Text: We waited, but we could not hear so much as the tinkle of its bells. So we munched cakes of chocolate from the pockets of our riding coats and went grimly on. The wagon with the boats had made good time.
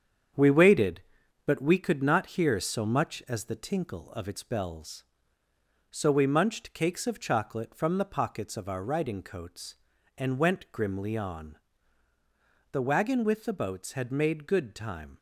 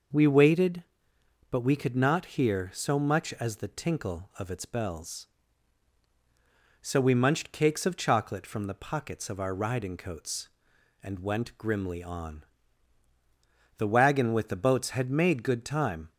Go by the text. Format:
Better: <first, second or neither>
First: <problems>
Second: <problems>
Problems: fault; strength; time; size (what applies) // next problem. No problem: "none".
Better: second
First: gets quieter; noticeable; throughout; 6 dB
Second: none